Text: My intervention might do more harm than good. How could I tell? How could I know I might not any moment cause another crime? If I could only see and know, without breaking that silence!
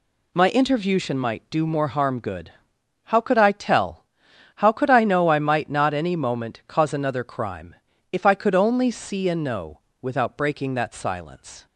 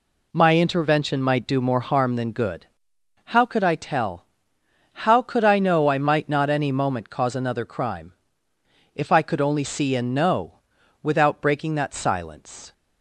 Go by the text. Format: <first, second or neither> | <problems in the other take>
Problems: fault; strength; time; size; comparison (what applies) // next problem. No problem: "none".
second | skips "than"; at 2.1 s